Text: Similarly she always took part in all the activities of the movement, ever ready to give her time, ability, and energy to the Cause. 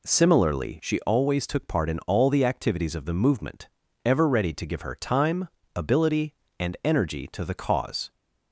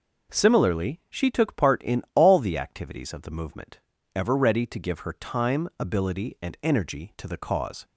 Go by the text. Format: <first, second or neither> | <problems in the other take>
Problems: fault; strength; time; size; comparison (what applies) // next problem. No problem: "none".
first | skips "always"; at 1.2 s